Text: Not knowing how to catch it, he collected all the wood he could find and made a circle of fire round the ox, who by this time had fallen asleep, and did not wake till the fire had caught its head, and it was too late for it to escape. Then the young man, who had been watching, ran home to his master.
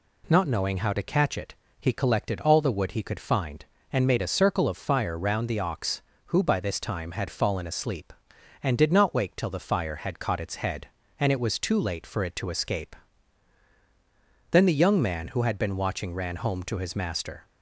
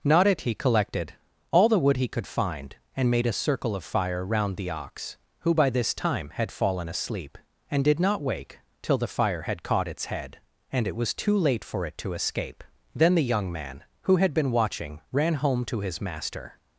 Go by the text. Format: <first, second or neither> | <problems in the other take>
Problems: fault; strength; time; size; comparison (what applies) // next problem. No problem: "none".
first | skips "knowing how to catch"; at 0.2 s // pauses between "collected" and "all"; at 1.1 s; 0.38 s long // pauses between "wake" and "till"; slight; at 8.5 s; 0.22 s long